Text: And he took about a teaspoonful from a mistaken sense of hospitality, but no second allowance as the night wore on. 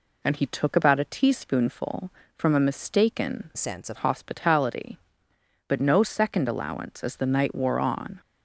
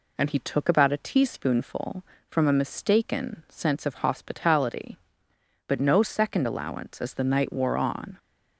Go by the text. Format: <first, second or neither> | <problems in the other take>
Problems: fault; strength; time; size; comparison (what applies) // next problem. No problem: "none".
second | changes voice from "sense" to "of"; from 3.5 to 3.9 s; 0.4 s long